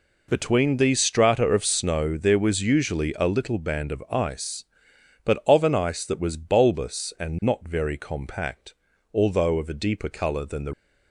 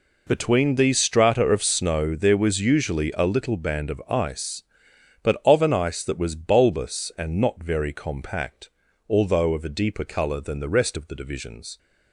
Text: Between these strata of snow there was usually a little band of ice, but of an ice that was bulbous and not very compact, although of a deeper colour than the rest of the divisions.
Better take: second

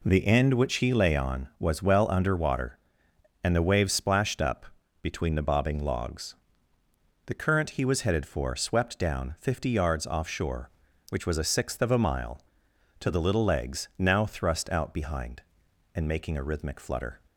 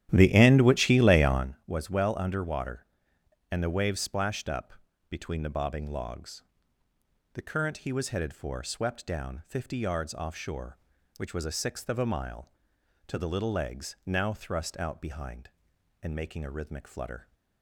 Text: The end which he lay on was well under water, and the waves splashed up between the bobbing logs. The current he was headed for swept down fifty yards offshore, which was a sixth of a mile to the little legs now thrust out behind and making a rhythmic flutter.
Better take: first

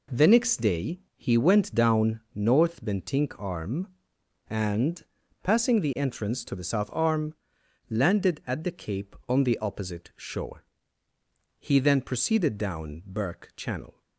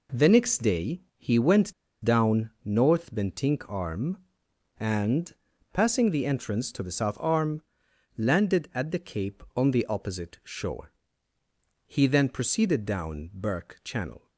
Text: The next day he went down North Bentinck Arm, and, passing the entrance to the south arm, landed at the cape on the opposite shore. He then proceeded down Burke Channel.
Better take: first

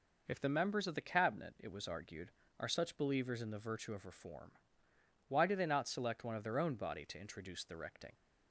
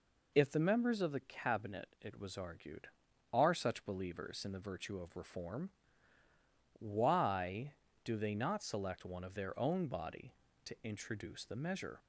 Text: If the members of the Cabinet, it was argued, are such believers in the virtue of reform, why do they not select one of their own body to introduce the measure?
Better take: second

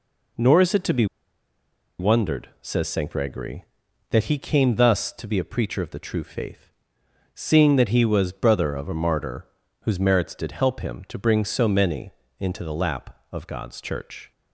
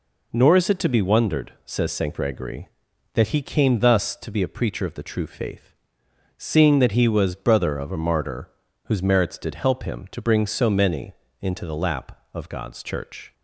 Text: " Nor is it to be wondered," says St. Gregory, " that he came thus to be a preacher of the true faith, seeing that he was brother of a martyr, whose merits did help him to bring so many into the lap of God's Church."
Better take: second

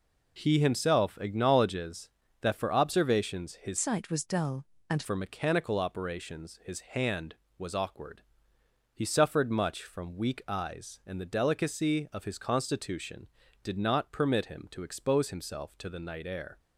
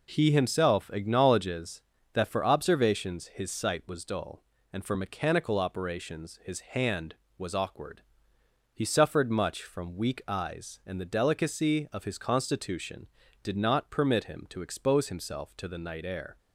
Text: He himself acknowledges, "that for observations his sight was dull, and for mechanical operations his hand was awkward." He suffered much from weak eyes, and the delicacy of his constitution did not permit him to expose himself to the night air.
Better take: second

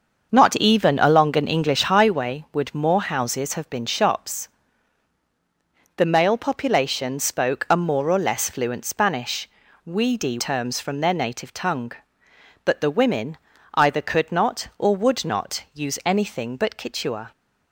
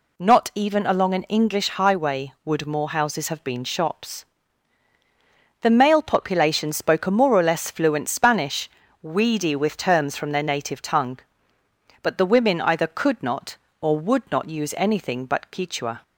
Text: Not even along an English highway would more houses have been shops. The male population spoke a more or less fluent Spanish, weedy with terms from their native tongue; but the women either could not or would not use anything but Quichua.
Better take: second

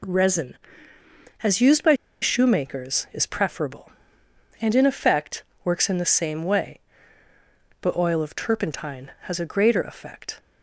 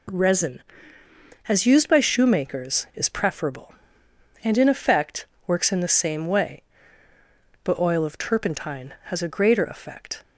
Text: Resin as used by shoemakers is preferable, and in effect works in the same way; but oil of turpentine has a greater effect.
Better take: second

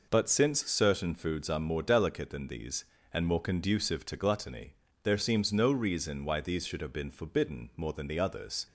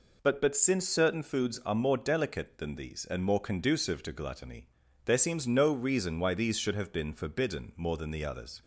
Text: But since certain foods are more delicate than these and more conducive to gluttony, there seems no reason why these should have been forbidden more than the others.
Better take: first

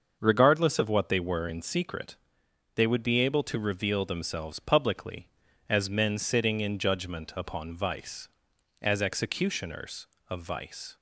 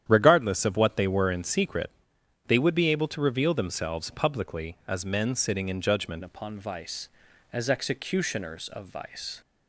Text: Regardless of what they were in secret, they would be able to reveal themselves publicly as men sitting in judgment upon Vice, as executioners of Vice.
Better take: first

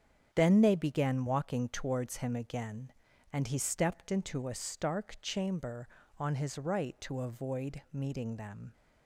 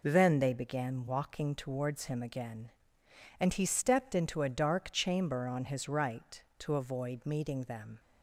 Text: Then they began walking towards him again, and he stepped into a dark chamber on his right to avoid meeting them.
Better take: second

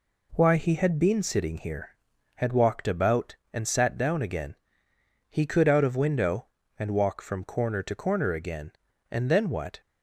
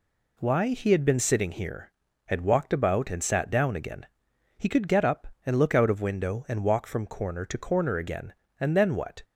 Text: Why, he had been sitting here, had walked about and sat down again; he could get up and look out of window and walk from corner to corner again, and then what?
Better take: second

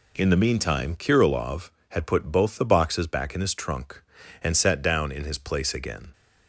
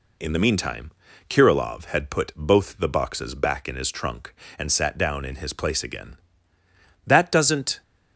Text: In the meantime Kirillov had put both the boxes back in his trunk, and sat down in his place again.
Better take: first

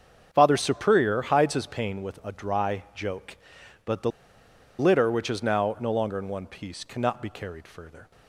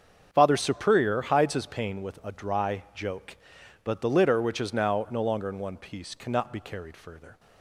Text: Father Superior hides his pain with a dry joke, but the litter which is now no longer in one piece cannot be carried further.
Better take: second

